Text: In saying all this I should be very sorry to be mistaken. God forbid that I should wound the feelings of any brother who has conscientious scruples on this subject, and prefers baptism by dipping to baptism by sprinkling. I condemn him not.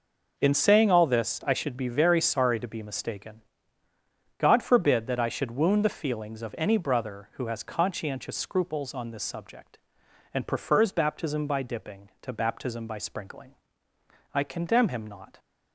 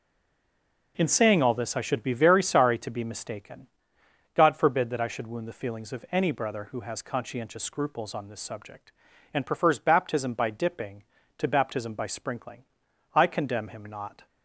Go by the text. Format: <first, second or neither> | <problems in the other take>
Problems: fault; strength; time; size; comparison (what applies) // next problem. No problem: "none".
first | stays silent before the first word; slight; until 0.9 s; 0.9 s long